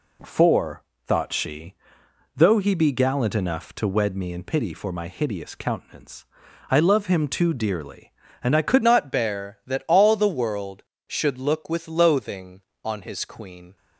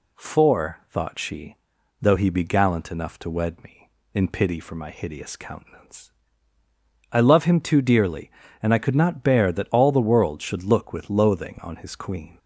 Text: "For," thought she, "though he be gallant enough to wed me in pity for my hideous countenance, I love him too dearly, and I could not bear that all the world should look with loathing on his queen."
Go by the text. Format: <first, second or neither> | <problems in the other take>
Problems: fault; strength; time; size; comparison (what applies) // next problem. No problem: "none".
second | changes voice at "not"; from 8.8 s on; 4.9 s long